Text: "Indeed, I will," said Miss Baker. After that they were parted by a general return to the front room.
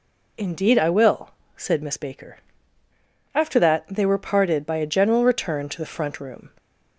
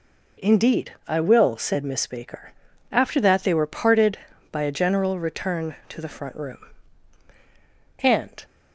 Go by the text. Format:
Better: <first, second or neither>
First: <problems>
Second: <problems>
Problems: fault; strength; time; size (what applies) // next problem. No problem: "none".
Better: first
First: none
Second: goes on to say "And"; slight; from 7.9 s on; 0.46 s long